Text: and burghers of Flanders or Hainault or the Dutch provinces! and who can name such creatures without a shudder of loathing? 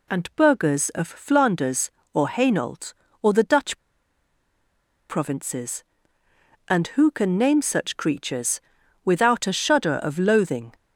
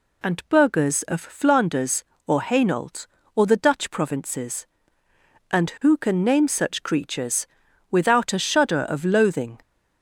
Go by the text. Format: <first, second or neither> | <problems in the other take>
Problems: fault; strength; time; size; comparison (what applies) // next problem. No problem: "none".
second | pauses between "Dutch" and "provinces"; strong; at 3.7 s; 1.3 s long // pauses between "creatures" and "without"; at 8.5 s; 0.44 s long; also in the second